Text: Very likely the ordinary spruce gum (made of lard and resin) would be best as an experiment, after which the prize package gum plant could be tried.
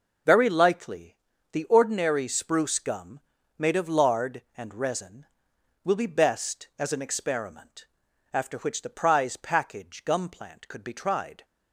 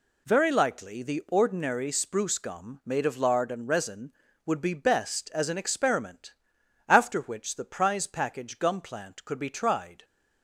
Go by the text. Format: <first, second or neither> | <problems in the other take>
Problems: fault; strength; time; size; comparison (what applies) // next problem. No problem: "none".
second | pauses between "likely" and "the"; slight; at 1.1 s; 0.36 s long // says "will" for "would"; at 5.8 s